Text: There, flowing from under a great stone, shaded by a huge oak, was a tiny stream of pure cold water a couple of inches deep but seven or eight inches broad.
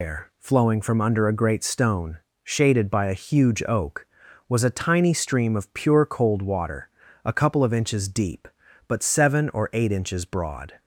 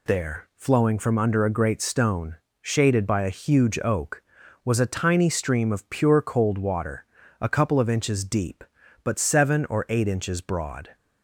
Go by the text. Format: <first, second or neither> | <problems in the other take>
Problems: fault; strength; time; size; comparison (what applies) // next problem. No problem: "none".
second | loses the start of "There"; at 0.0 s; 120 ms // pauses between "water" and "a"; slight; at 6.8 s; 0.36 s long; slight in the second